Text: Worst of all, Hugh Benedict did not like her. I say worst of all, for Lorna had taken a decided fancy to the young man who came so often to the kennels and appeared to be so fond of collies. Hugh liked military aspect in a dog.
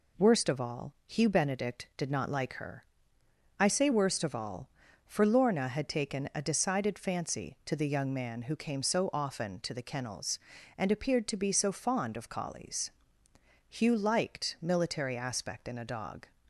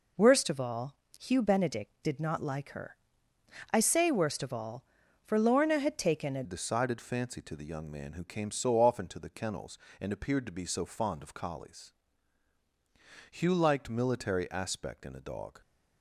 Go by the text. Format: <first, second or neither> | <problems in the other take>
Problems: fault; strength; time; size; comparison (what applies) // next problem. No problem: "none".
first | changes voice at "decided"; from 6.4 s on; 9.2 s long